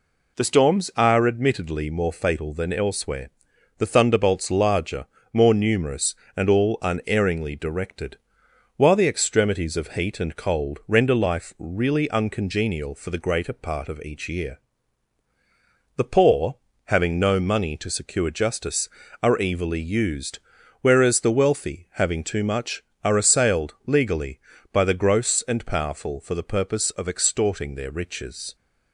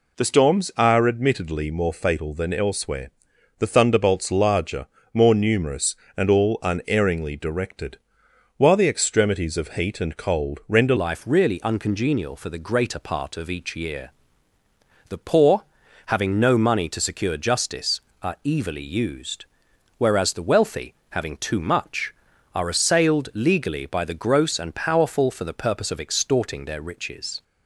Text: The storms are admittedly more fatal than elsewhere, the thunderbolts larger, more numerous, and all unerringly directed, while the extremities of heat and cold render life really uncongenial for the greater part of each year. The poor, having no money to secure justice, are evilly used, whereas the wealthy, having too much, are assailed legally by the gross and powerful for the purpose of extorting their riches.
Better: first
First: none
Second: changes voice at "life"; from 10.9 s on; 16.5 s long

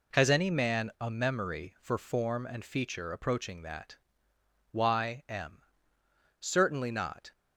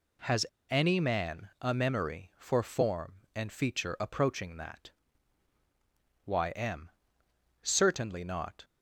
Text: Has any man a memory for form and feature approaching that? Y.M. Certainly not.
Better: first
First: none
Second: pauses between "Has" and "any"; slight; at 0.4 s; 0.27 s long

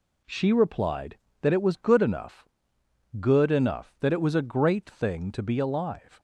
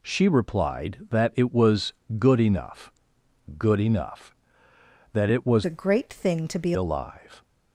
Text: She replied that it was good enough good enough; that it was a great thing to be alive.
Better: first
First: pauses between "enough" and "good"; noticeable; at 2.4 s; 0.72 s long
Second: pauses between "was" and "good"; slight; at 1.9 s; 0.24 s long // pauses between "enough" and "good"; noticeable; at 2.9 s; 0.68 s long // changes voice from "a" to "be"; from 5.6 to 6.7 s; 1.1 s long

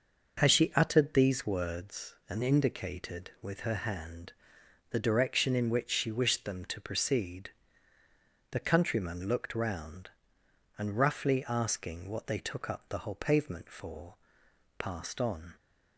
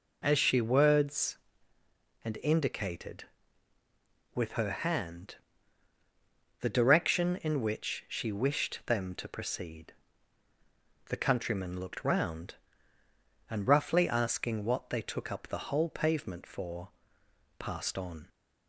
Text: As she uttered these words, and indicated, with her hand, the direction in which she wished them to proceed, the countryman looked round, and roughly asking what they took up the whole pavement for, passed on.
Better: first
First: none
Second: skips "uttered these"; at 0.6 s

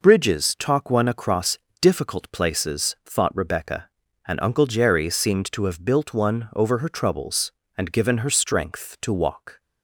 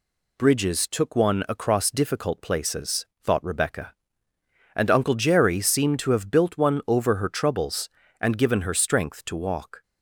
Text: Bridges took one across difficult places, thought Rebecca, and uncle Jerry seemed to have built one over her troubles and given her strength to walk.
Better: second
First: says "talk" for "took"; at 0.5 s // pauses between "across" and "difficult"; slight; at 1.5 s; 0.20 s long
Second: none

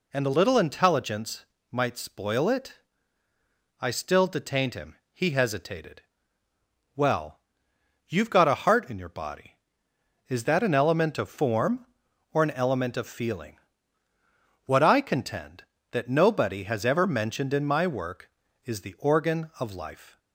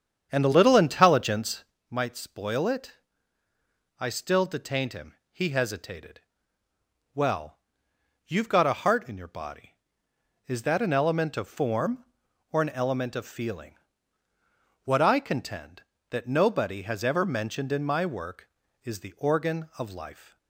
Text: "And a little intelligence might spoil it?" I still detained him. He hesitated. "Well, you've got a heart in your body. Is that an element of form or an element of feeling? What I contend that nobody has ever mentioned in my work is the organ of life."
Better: first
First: pauses between "intelligence" and "might"; slight; at 1.4 s; 0.26 s long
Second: starts louder than the rest; strong; until 1.8 s; 8 dB // pauses between "intelligence" and "might"; slight; at 1.6 s; 0.26 s long

